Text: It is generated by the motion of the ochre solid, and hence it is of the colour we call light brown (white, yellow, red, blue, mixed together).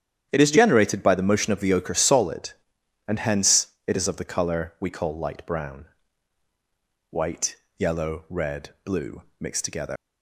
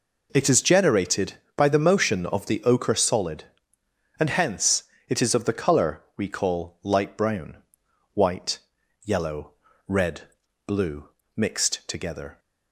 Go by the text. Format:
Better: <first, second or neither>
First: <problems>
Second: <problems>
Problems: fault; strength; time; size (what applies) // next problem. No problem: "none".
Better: second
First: starts louder than the rest; strong; until 1.3 s; 9.5 dB // pauses between "hence" and "it"; slight; at 3.6 s; 0.18 s long // leaves "together" unfinished; at 9.9 s; 125 ms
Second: pauses between "hence" and "it"; slight; at 4.8 s; 0.24 s long